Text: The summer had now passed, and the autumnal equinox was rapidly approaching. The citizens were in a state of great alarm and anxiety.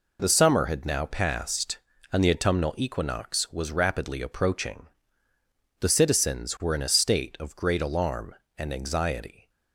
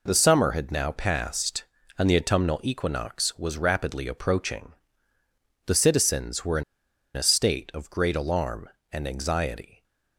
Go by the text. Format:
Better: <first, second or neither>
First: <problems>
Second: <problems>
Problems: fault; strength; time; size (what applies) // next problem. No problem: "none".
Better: first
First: none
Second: pauses between "in" and "a"; noticeable; at 6.6 s; 0.51 s long